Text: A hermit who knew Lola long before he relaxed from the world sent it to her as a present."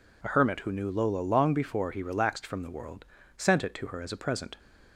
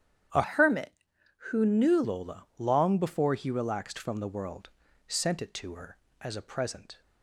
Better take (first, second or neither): first